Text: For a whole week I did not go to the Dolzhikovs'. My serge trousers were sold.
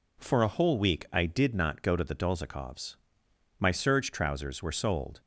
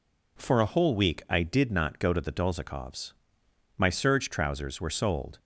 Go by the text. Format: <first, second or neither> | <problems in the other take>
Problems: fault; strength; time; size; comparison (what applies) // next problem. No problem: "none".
neither | none